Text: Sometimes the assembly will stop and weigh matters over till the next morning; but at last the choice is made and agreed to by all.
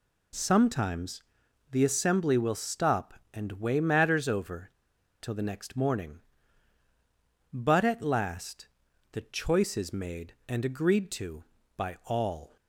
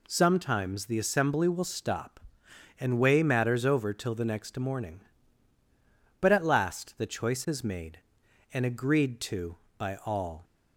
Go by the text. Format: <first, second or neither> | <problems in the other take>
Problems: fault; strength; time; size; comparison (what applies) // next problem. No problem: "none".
second | pauses between "Sometimes" and "the"; noticeable; at 1.2 s; 0.48 s long // pauses between "over" and "till"; noticeable; at 4.7 s; 0.47 s long // pauses between "last" and "the"; noticeable; at 8.6 s; 0.46 s long